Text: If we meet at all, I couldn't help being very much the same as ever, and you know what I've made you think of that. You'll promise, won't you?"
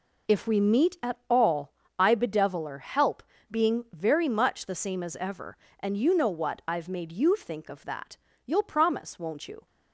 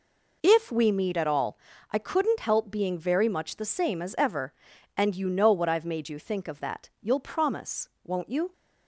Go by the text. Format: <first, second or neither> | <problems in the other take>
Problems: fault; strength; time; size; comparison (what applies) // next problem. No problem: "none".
second | says "bedeviler" for "couldn't"; at 2.1 s // pauses between "help" and "being"; slight; at 3.2 s; 0.28 s long